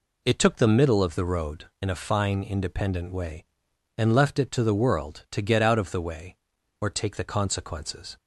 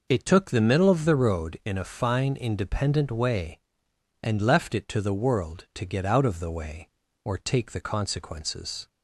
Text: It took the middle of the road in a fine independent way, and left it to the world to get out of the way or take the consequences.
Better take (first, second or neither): neither